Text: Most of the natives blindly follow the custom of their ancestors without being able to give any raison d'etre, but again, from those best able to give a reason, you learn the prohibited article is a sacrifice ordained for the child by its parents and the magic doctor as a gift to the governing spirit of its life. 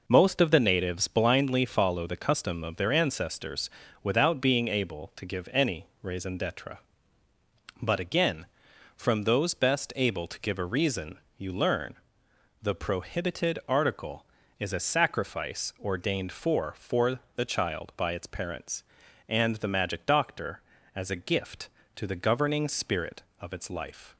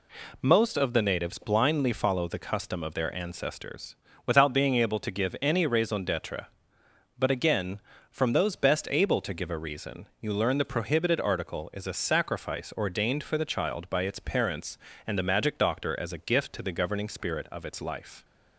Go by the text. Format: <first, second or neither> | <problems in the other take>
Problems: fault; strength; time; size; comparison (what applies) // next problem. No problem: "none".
second | pauses between "ancestors" and "without"; slight; at 3.7 s; 0.32 s long; slight in the second // pauses between "any" and "raison"; slight; at 5.8 s; 0.16 s long // pauses between "learn" and "the"; noticeable; at 11.9 s; 0.66 s long // says "for" twice; at 16.7 s